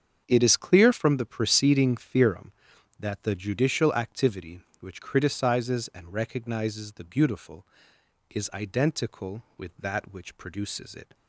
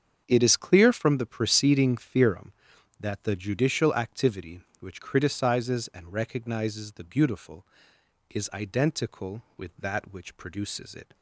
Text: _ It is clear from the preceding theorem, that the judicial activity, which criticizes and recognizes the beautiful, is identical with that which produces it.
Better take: neither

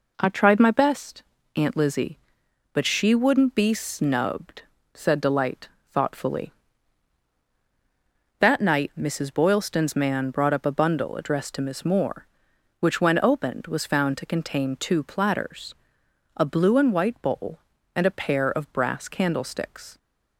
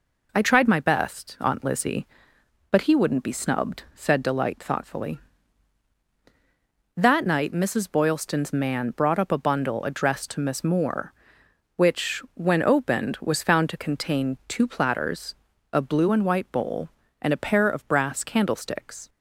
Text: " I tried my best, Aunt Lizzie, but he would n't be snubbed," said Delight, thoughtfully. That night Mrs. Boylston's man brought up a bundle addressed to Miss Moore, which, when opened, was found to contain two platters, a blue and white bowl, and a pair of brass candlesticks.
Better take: second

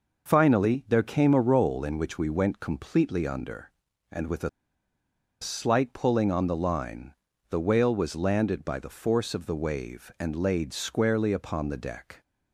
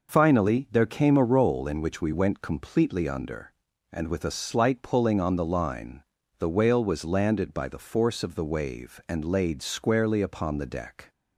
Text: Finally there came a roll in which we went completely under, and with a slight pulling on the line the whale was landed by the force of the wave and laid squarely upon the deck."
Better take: second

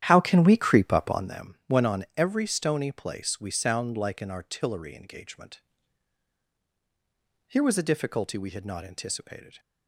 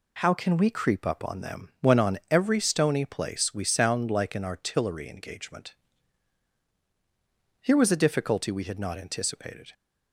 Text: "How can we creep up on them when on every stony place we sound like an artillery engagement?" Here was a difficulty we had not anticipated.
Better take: second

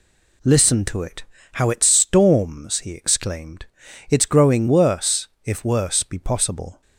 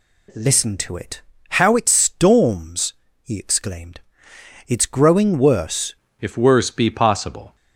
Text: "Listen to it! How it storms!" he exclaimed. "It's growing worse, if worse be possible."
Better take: first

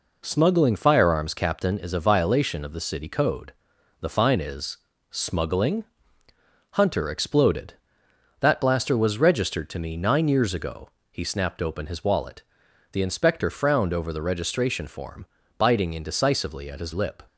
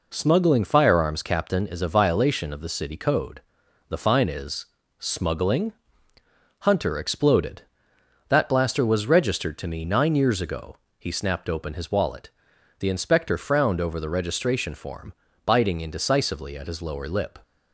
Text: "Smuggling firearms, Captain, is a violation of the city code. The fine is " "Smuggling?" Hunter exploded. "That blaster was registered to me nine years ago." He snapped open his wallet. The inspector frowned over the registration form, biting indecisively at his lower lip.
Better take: second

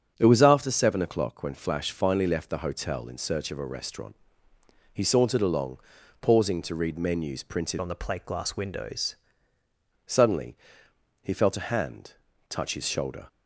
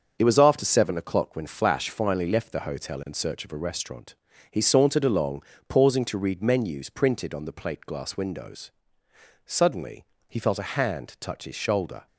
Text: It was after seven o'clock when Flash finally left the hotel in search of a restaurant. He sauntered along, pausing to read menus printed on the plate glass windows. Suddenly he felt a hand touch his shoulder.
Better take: second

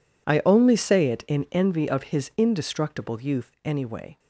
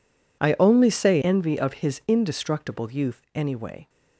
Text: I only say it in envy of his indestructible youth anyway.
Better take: first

